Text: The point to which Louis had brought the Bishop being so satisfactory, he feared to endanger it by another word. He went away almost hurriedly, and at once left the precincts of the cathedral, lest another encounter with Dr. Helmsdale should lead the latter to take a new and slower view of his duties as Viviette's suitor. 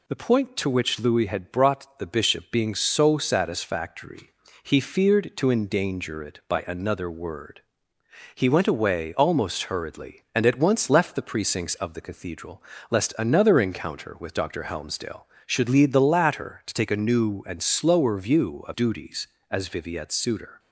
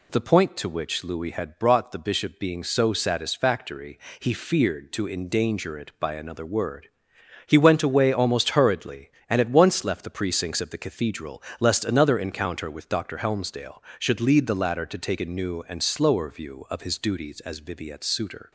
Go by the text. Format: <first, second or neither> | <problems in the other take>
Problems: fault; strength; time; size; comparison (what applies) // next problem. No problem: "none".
second | skips "his"; at 18.7 s